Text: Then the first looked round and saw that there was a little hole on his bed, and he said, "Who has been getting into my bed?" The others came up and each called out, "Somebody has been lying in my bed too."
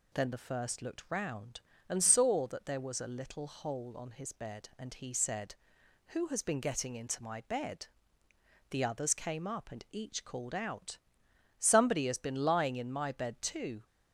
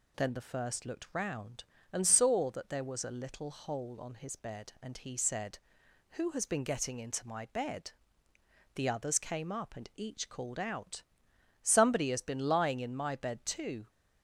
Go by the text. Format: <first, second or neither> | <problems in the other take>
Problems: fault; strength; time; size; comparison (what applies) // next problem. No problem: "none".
neither | none